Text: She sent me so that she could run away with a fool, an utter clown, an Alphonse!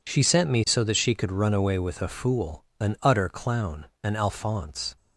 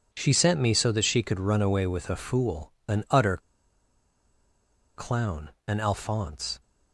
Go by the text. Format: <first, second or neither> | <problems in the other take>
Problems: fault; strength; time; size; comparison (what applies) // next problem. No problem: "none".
first | pauses between "utter" and "clown"; strong; at 3.3 s; 1.5 s long